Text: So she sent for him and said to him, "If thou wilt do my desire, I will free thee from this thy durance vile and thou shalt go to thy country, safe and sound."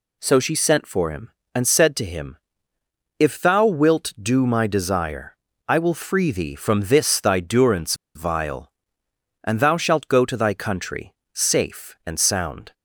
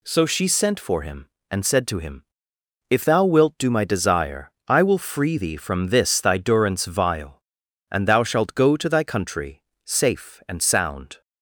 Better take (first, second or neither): second